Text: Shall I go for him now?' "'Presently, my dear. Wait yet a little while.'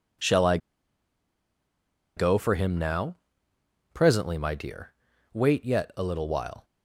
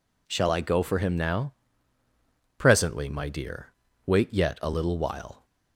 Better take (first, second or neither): second